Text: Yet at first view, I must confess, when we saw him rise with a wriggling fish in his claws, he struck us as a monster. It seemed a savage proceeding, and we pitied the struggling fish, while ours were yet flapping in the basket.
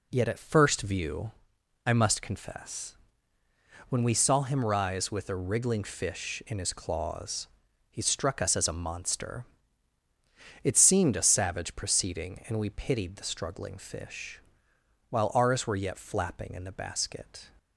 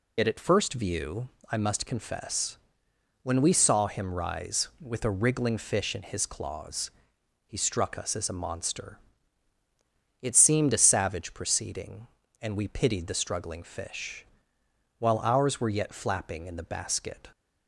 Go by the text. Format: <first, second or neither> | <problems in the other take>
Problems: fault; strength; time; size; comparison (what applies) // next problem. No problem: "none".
first | loses the start of "Yet"; at 0.1 s; 60 ms